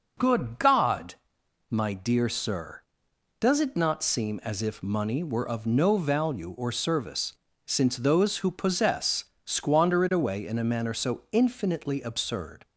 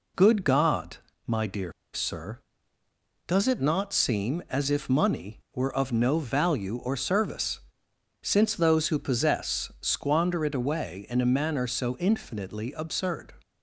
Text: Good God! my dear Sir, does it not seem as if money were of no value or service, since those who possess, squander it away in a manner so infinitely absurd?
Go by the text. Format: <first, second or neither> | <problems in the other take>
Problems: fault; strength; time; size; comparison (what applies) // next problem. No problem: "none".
first | pauses between "dear" and "Sir"; slight; at 1.7 s; 0.21 s long